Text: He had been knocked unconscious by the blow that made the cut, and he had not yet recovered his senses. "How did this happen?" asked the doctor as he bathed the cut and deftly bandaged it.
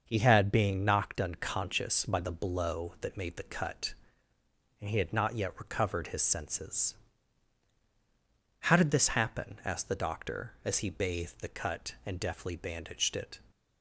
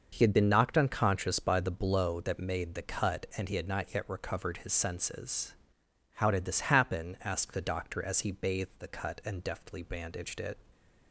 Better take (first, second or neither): second